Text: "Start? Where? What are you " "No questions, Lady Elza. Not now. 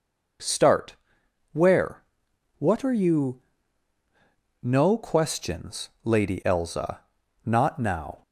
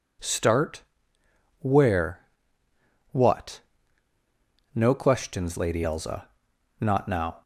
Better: first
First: none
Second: skips "are you"; at 3.8 s

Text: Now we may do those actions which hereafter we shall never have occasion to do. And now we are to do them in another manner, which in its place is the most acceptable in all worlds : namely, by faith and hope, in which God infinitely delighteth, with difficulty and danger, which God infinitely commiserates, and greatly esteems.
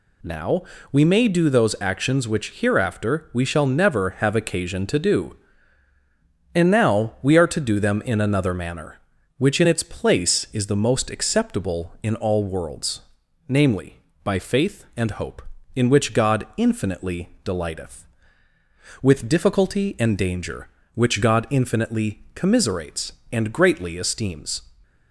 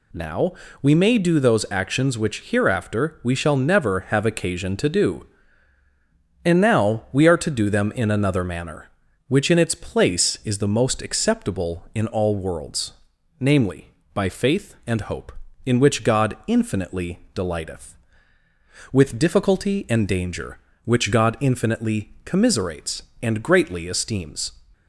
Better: neither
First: pauses between "Now" and "we"; slight; at 0.6 s; 0.30 s long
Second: pauses between "Now" and "we"; slight; at 0.5 s; 0.30 s long

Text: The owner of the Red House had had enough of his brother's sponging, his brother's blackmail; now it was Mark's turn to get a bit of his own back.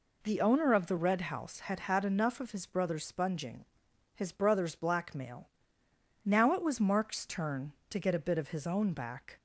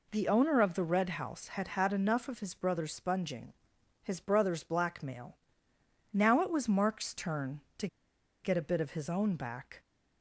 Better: first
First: none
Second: pauses between "to" and "get"; noticeable; at 7.8 s; 0.57 s long

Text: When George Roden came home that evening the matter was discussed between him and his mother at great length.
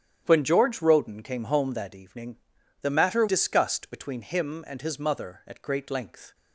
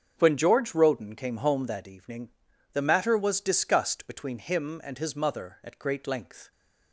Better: second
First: starts louder than the rest; strong; until 1.2 s; 9.5 dB // pauses between "evening" and "the"; at 2.3 s; 0.42 s long // skips "was"; at 3.2 s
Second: starts louder than the rest; strong; until 1.1 s; 7 dB // pauses between "evening" and "the"; at 2.3 s; 0.40 s long

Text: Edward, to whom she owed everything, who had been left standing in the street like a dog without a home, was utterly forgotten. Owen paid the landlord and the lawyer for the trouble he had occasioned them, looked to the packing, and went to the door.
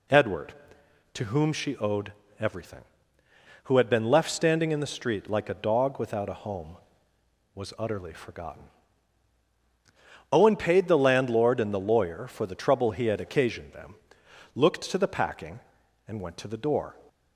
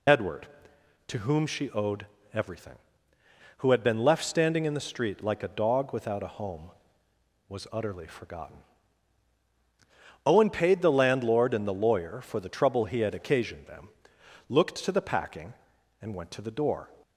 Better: first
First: pauses between "owed" and "everything"; slight; at 2.1 s; 0.26 s long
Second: loses the start of "Edward"; at 0.0 s; 35 ms // pauses between "owed" and "everything"; slight; at 2.0 s; 0.26 s long

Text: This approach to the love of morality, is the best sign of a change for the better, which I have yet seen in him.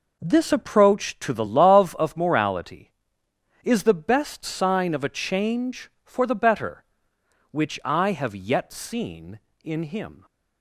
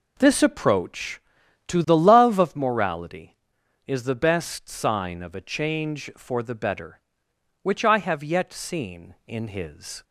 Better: first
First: none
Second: says "his" for "him"; at 9.4 s

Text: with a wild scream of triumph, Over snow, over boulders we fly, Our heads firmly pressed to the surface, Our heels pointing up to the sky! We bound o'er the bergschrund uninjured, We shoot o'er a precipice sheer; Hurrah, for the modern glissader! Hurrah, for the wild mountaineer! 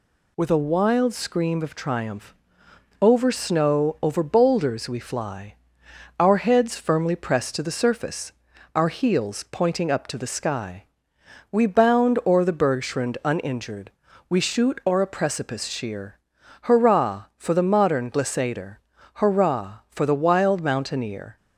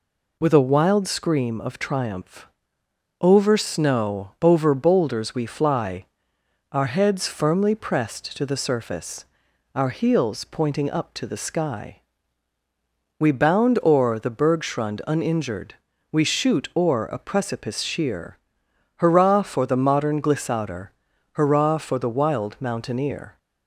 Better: neither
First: none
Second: none

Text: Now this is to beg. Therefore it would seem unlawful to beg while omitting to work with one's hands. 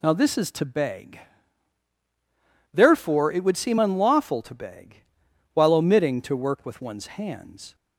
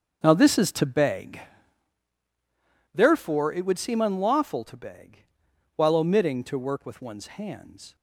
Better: first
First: pauses between "beg" and "while"; noticeable; at 5.0 s; 0.52 s long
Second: starts louder than the rest; until 1.9 s; 6.5 dB // pauses between "beg" and "while"; noticeable; at 5.2 s; 0.52 s long

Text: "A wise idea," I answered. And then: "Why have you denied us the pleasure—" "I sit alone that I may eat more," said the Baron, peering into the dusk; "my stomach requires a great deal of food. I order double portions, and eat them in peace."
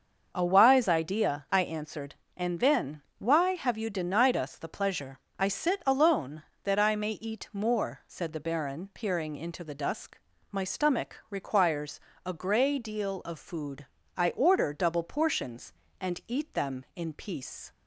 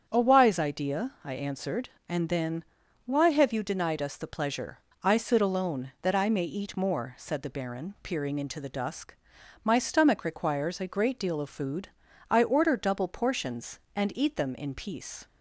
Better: second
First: starts louder than the rest; until 1.3 s; 6.5 dB // pauses between "requires" and "a"; slight; at 12.0 s; 0.24 s long // says "grey" for "great"; at 12.3 s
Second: starts louder than the rest; strong; until 1.0 s; 7.5 dB

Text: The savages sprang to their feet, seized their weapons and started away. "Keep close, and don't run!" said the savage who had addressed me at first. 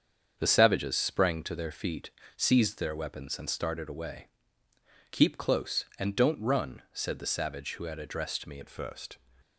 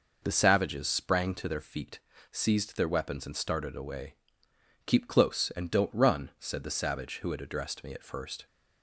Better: second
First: starts louder than the rest; strong; until 1.3 s; 7 dB // changes voice at "at"; from 8.6 s on; 0.5 s long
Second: none

